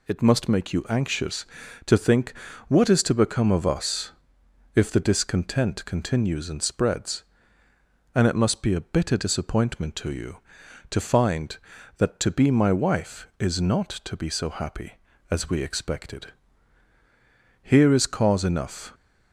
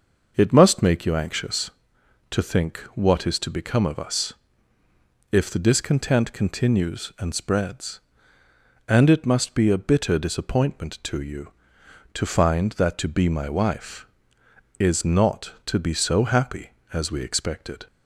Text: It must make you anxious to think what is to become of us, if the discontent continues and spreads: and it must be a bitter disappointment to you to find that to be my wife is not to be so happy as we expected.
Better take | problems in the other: second | pauses between "think" and "what"; slight; at 2.3 s; 0.34 s long; slight in the second // goes on to say "Here is cause enough"; from 17.6 s on; 1.3 s long

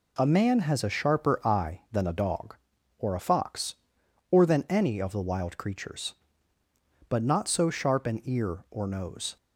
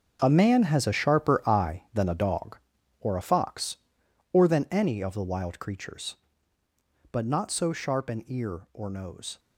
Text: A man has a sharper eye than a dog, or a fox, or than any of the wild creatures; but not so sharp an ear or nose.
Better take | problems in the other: first | gets quieter; strong; throughout; 12.5 dB

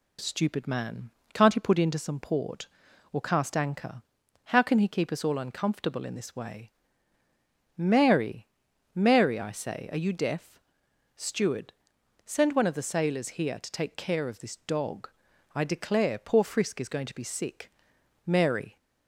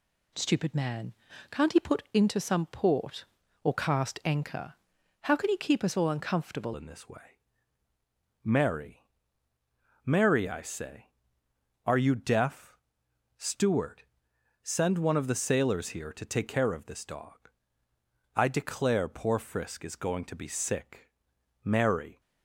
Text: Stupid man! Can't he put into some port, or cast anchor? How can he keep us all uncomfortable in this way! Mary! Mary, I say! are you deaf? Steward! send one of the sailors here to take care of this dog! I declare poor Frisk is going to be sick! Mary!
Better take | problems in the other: first | changes voice at "in"; from 6.7 s on; 15.4 s long

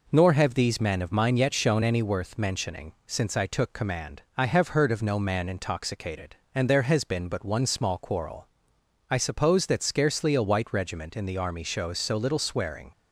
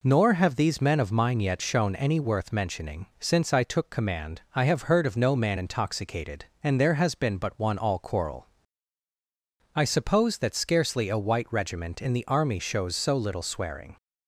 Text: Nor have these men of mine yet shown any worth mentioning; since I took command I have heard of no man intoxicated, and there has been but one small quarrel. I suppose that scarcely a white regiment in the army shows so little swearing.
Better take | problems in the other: first | says "all" for "small"; at 7.7 s

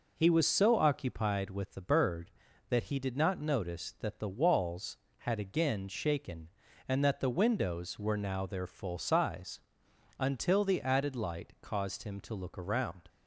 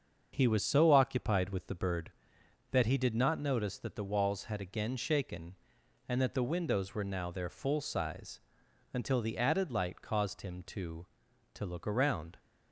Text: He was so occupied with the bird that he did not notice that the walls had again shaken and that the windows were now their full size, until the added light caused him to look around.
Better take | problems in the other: first | starts louder than the rest; until 1.3 s; 7 dB // says "to" twice; at 11.5 s

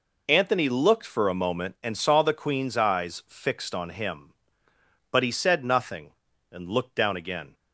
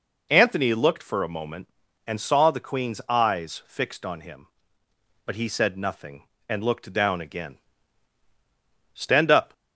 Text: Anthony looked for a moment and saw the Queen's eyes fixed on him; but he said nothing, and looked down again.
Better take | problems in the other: first | goes on to say "Stand up"; from 8.9 s on; 0.60 s long

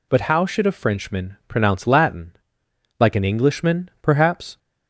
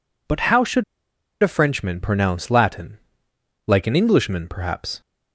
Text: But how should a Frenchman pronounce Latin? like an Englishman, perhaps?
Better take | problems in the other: first | pauses between "should" and "a"; noticeable; at 0.8 s; 0.58 s long

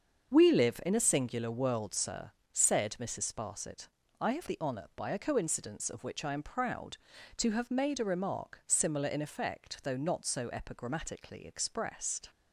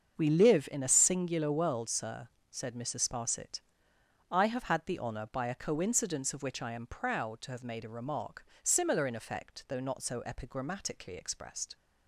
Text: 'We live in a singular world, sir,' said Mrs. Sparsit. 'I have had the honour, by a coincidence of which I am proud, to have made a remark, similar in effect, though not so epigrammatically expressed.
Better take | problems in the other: second | starts louder than the rest; until 1.3 s; 6.5 dB; also in the second // skips "had"; at 4.4 s

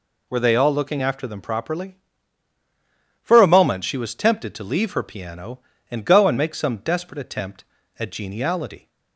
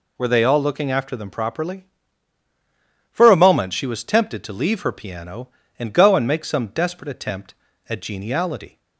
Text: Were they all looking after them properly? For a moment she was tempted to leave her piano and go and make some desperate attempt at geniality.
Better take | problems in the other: neither | none

